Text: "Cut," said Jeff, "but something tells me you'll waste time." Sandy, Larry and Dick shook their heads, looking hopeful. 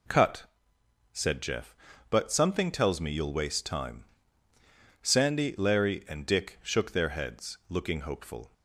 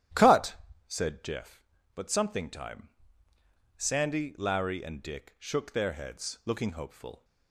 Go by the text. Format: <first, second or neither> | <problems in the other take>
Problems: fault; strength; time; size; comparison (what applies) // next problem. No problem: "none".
first | starts louder than the rest; strong; until 1.4 s; 12.5 dB // skips "tells me you'll waste"; at 2.5 s